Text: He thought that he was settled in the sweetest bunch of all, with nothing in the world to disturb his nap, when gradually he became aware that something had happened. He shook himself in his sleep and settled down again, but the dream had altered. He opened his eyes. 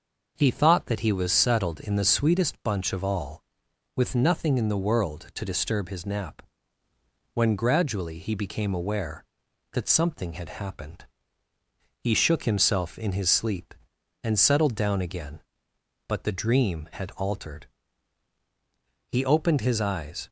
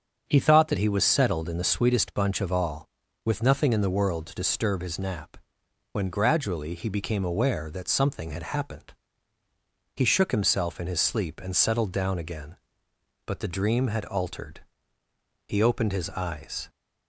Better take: neither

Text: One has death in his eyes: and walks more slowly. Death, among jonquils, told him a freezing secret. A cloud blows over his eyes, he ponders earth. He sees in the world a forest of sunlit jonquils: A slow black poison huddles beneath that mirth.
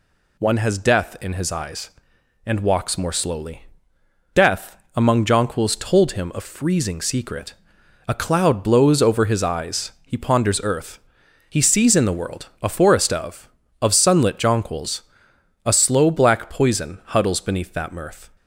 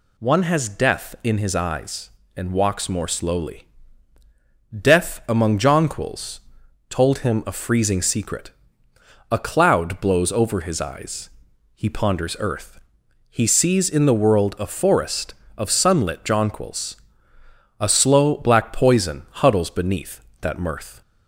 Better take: second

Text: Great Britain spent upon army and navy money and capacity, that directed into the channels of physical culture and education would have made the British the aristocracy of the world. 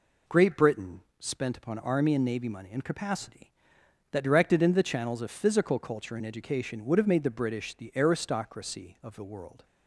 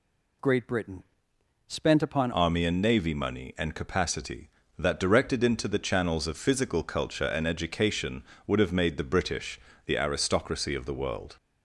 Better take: first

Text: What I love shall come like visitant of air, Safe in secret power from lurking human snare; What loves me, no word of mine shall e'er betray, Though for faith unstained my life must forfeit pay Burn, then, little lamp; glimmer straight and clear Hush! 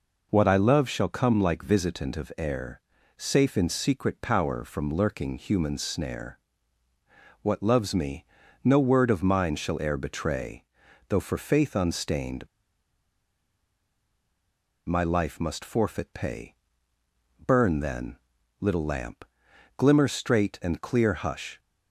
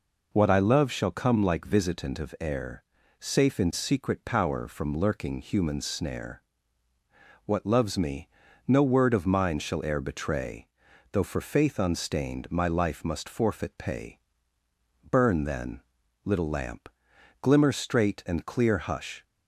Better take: second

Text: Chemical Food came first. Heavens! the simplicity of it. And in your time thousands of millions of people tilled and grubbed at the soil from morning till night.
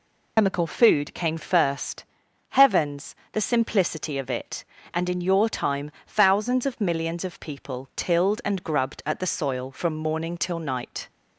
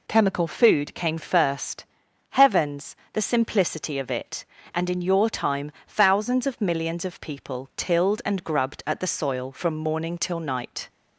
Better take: second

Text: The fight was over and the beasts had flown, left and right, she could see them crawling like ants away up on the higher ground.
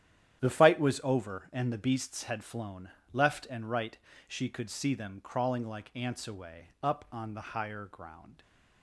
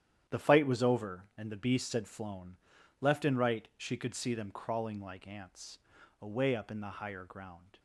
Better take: first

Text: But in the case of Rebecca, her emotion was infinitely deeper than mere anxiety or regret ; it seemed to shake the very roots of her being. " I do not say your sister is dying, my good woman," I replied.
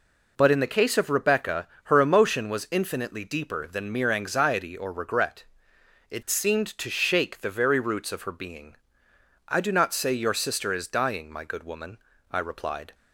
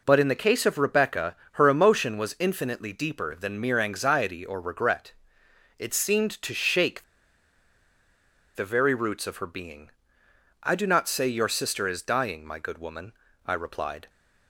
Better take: first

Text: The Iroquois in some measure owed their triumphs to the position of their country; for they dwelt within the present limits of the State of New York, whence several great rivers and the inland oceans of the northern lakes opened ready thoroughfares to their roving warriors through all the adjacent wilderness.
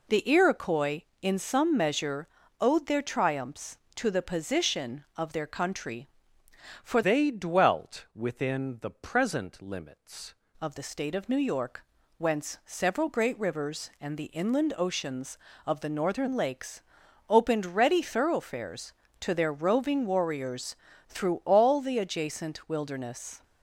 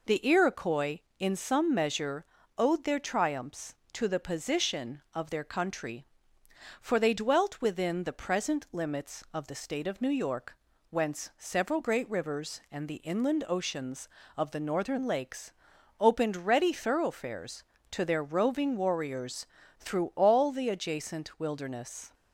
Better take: second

